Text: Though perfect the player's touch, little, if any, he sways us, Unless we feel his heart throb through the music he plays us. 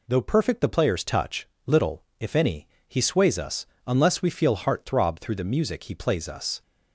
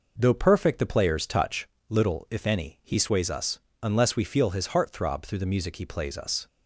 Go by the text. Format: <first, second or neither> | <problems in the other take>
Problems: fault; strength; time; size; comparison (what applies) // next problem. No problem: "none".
second | skips "his"; at 4.5 s